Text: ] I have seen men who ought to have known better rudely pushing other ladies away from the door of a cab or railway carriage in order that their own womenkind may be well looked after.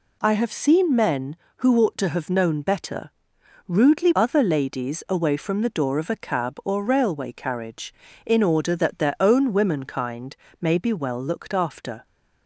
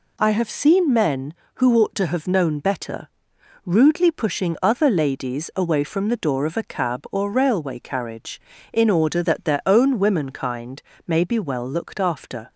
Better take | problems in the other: second | pauses between "better" and "rudely"; noticeable; at 3.1 s; 0.58 s long; noticeable in the second // skips "pushing"; at 4.1 s // pauses between "womenkind" and "may"; slight; at 10.3 s; 0.28 s long; slight in the second

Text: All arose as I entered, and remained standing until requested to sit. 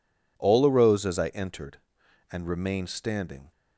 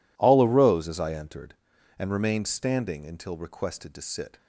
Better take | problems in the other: second | stops before "until requested to sit"; at 3.5 s

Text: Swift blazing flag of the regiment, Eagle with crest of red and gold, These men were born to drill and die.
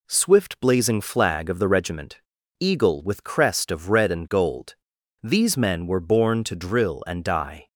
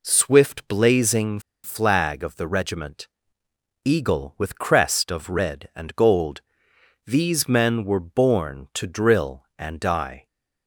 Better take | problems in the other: first | pauses between "blazing" and "flag"; slight; at 1.4 s; 0.23 s long

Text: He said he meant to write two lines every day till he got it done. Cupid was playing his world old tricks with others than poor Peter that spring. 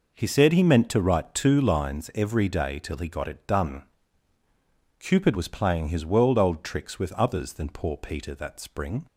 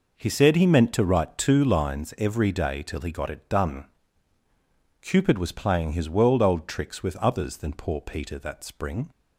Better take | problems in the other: neither | none

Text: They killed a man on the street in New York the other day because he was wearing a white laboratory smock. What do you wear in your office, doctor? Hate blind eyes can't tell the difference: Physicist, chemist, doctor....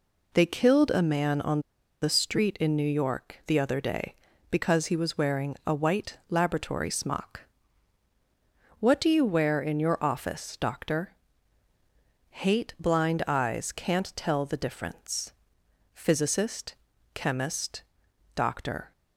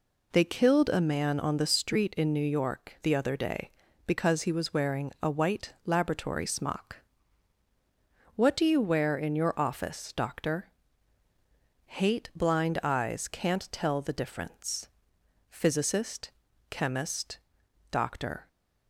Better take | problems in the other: second | pauses between "on" and "the"; at 1.5 s; 0.41 s long

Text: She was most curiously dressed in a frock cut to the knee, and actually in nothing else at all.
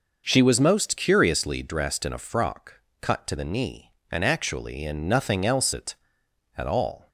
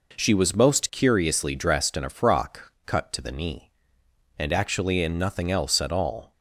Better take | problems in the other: second | pauses between "frock" and "cut"; slight; at 2.8 s; 0.20 s long // says "at" twice; at 6.5 s

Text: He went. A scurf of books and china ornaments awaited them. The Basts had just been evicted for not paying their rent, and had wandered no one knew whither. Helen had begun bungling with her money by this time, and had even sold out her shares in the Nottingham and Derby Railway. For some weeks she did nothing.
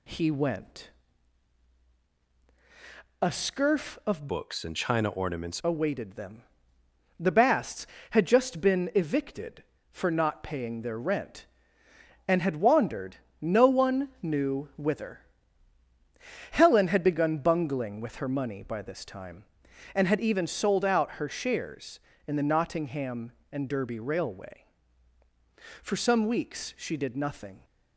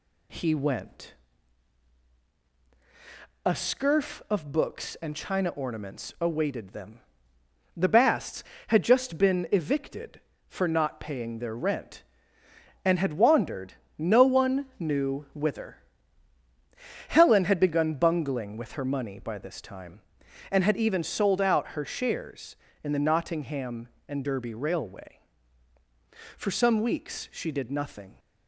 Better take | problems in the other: second | changes voice from "books" to "ornaments"; from 4.2 to 5.5 s; 1.3 s long // pauses between "wandered" and "no"; slight; at 13.1 s; 0.24 s long; slight in the second

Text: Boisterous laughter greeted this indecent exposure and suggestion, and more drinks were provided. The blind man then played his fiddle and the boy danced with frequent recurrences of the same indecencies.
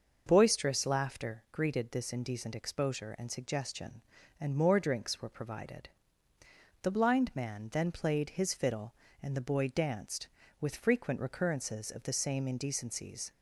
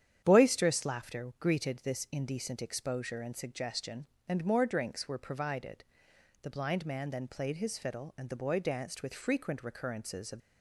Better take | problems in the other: first | starts louder than the rest; strong; until 1.2 s; 9.5 dB; noticeable in the first // stops before "the same indecencies"; at 10.4 s

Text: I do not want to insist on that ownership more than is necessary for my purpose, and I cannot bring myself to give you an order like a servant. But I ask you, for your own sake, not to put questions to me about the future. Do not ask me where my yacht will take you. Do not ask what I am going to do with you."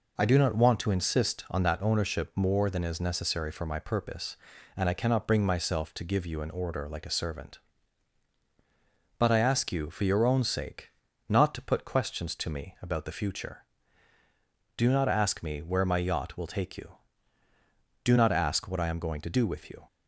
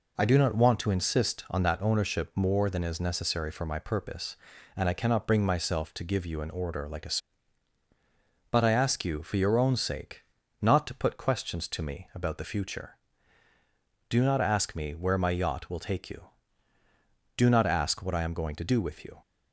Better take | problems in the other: first | skips "servant"; at 7.8 s

